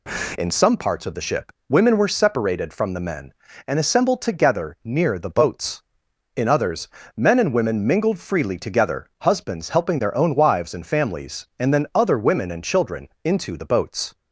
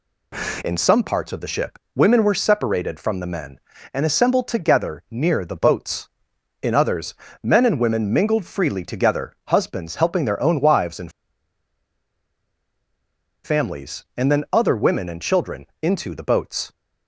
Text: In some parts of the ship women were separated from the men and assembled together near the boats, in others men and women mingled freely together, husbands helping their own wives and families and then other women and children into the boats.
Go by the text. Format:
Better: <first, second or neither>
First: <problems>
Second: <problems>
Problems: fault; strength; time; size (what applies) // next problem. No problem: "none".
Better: first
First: pauses between "ship" and "women"; slight; at 1.5 s; 0.16 s long // pauses between "others" and "men"; slight; at 6.8 s; 0.30 s long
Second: pauses between "ship" and "women"; slight; at 1.7 s; 0.16 s long // pauses between "others" and "men"; slight; at 7.1 s; 0.30 s long // pauses between "and" and "families"; strong; at 11.1 s; 2.3 s long